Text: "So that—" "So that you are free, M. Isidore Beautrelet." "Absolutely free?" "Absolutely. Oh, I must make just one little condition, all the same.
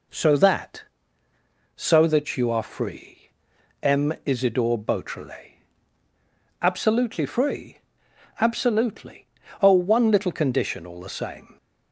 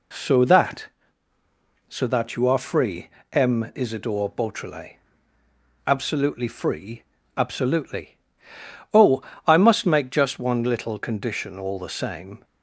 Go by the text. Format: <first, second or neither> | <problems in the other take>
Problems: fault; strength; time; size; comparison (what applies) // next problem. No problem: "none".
second | skips "I must make just"; at 9.7 s